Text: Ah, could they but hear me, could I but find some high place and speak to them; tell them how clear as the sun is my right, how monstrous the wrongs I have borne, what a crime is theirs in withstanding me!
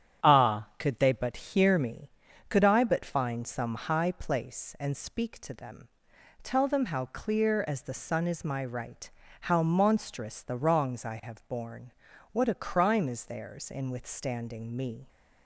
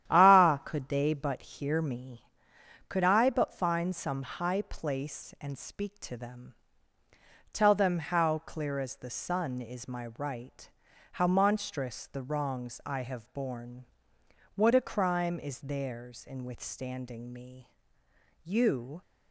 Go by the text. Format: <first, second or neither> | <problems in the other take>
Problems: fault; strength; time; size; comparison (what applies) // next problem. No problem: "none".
first | starts louder than the rest; strong; until 1.1 s; 11 dB; strong in the first // goes on to say "You"; from 18.4 s on; 0.58 s long